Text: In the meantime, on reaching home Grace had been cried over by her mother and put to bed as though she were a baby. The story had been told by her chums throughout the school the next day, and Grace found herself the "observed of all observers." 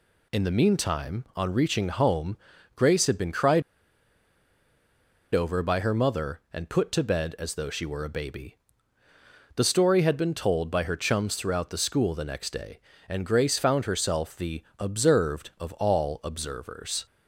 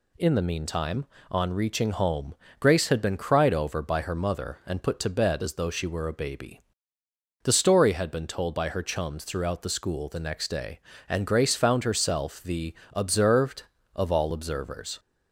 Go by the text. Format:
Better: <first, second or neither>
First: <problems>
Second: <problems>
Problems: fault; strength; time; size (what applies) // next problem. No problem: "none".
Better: second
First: pauses between "home" and "Grace"; at 2.3 s; 0.38 s long // pauses between "cried" and "over"; strong; at 3.6 s; 1.7 s long // pauses between "the" and "observed"; slight; at 14.6 s; 0.16 s long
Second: pauses between "home" and "Grace"; slight; at 2.3 s; 0.24 s long // pauses between "the" and "observed"; slight; at 12.7 s; 0.20 s long